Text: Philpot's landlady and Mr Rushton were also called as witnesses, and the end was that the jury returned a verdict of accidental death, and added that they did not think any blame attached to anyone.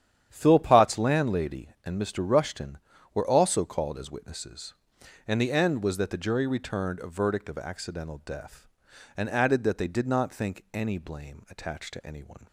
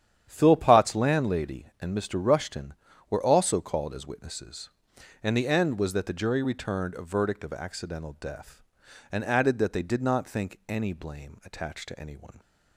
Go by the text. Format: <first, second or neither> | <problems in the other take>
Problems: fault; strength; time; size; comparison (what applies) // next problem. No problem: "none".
neither | starts louder than the rest; strong; the same in both